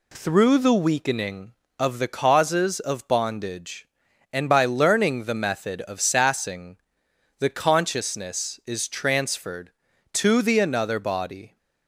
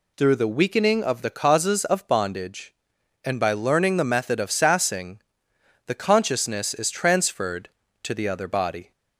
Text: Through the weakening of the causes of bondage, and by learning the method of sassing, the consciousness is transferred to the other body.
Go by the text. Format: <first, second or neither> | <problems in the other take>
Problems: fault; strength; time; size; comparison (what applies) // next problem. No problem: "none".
second | says "another" for "other"; at 10.6 s